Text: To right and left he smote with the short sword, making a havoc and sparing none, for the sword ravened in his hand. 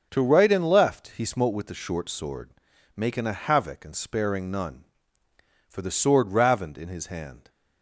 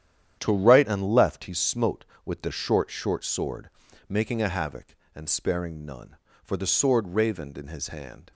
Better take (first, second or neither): first